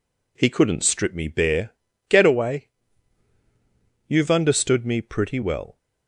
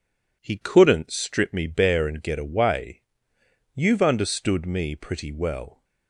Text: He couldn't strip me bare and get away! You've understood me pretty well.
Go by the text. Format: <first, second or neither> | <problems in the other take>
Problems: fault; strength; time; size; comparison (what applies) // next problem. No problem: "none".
second | skips "and"; at 1.9 s